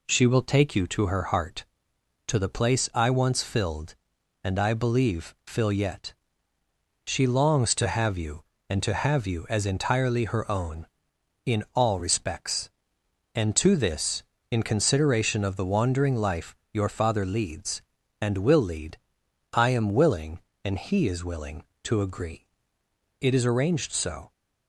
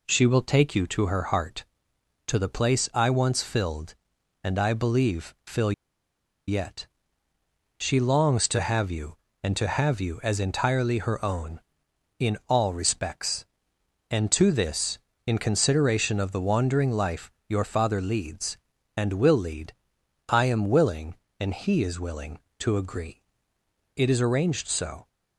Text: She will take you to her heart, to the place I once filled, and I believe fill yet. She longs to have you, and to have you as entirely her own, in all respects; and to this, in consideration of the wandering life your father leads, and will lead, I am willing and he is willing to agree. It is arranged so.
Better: first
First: pauses between "life" and "your"; slight; at 16.5 s; 0.18 s long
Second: pauses between "fill" and "yet"; noticeable; at 5.7 s; 0.75 s long // pauses between "life" and "your"; slight; at 17.2 s; 0.18 s long

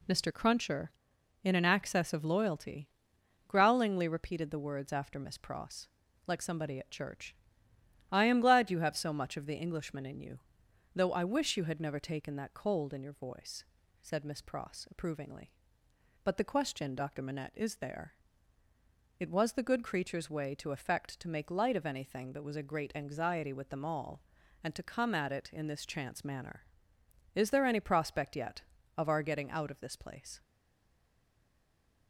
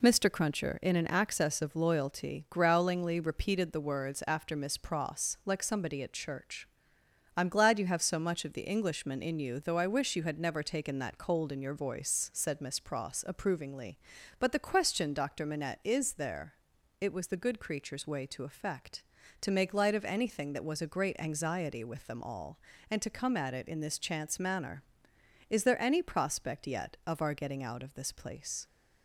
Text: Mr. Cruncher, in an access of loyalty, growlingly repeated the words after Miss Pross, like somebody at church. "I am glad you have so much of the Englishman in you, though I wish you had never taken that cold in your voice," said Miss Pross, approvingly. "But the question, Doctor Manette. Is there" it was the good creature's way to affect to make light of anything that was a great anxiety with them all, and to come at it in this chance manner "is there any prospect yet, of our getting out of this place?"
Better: second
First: pauses between "there" and "it"; at 18.1 s; 1.0 s long // stays silent after the last word; noticeable; from 30.4 s on; 1.6 s long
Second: pauses between "there" and "it"; at 16.5 s; 0.44 s long

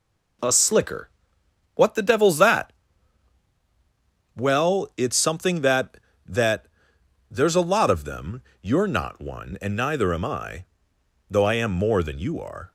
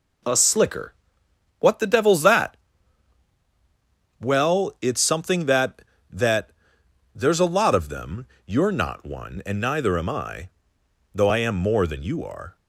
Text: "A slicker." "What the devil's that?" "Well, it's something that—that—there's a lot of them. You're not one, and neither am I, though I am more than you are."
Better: neither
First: none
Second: none

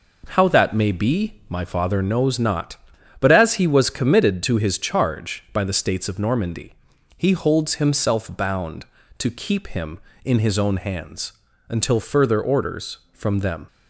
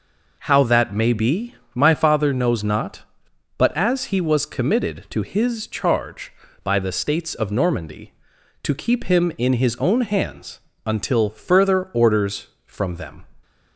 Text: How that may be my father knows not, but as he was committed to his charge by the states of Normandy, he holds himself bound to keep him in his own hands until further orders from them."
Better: first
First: pauses between "hands" and "until"; slight; at 11.3 s; 0.36 s long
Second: pauses between "be" and "my"; slight; at 1.5 s; 0.20 s long // skips "he holds himself bound"; at 8.3 s // pauses between "hands" and "until"; slight; at 10.5 s; 0.28 s long

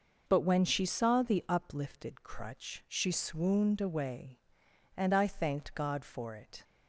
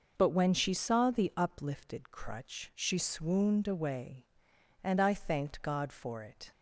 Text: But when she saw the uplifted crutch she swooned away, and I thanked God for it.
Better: neither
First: none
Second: none

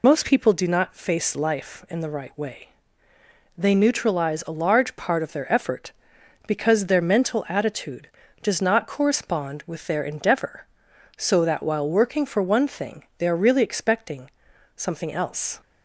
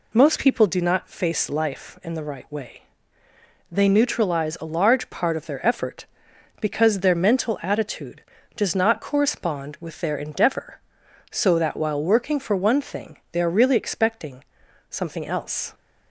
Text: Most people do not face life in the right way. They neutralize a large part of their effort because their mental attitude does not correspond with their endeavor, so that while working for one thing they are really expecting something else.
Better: second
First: loses the start of "Most"; at 0.0 s; 40 ms // pauses between "expecting" and "something"; noticeable; at 14.3 s; 0.46 s long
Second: pauses between "expecting" and "something"; noticeable; at 14.4 s; 0.46 s long

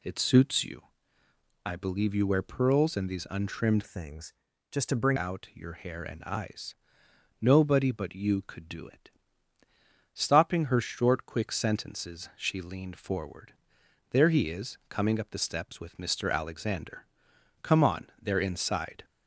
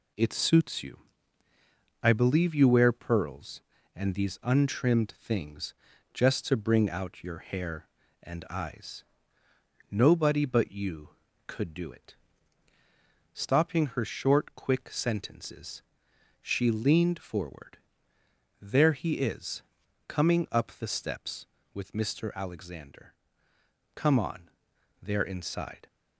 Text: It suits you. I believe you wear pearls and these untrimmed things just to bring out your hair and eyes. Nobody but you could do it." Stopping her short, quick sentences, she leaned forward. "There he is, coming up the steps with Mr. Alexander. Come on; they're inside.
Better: second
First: changes voice from "things" to "bring"; from 3.8 to 5.1 s; 1.3 s long // pauses between "things" and "just"; slight; at 4.3 s; 0.36 s long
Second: pauses between "things" and "just"; at 5.7 s; 0.40 s long

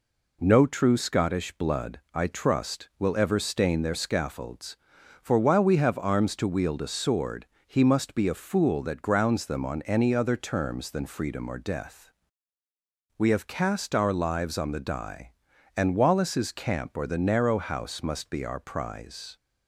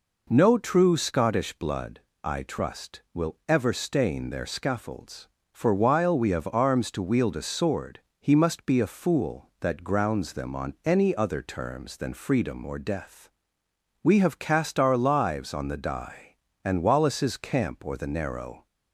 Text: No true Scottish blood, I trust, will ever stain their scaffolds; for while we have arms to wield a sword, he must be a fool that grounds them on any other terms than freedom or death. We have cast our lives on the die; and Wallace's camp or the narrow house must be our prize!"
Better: first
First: none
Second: stops before "house must be our prize"; at 18.6 s

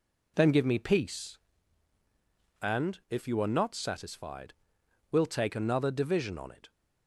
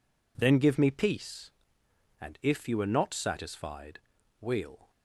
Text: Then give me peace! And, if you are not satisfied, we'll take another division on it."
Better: first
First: none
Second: stops before "take another division on it"; at 4.9 s

